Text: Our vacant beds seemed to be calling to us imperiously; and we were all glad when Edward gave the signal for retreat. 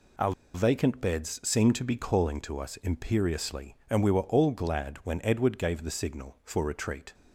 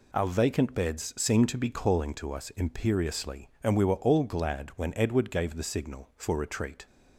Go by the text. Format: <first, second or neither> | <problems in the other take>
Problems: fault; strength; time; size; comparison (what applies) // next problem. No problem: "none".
second | pauses between "Our" and "vacant"; slight; at 0.3 s; 0.22 s long